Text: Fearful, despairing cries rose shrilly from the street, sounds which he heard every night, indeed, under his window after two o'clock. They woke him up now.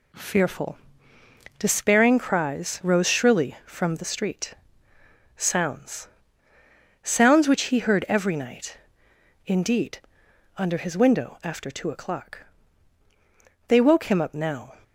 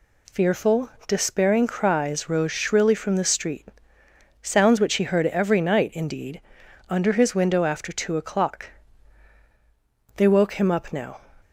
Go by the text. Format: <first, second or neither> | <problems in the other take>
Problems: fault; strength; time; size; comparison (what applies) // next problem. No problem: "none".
second | says "sounds" twice; at 7.0 s